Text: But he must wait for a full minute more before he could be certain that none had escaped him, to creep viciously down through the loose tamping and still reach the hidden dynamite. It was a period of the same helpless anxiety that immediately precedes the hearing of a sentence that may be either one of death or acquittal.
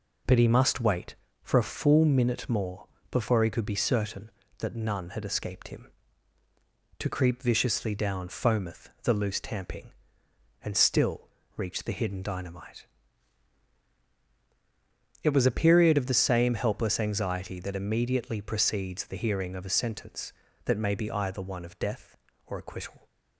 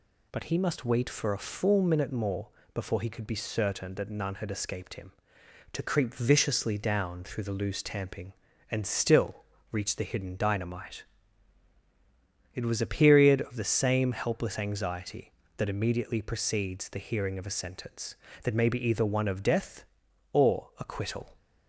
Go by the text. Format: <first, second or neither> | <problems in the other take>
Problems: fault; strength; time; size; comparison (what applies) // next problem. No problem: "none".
second | pauses between "more" and "before"; slight; at 2.8 s; 0.24 s long; slight in the second // says "foameth" for "through"; at 8.2 s // pauses between "still" and "reach"; slight; at 11.2 s; 0.28 s long; slight in the second